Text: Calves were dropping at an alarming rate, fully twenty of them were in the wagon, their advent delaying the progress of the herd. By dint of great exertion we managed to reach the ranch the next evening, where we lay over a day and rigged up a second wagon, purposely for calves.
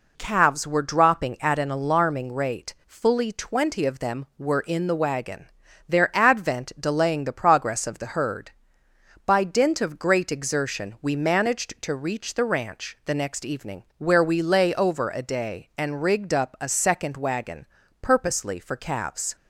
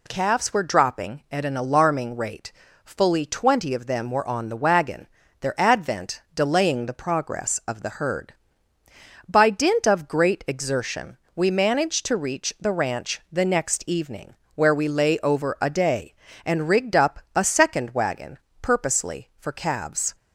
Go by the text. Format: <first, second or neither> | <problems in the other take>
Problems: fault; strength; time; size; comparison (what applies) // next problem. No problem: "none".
first | says "on" for "in"; at 4.2 s // pauses between "exertion" and "we"; slight; at 11.1 s; 0.18 s long // pauses between "up" and "a"; slight; at 17.1 s; 0.16 s long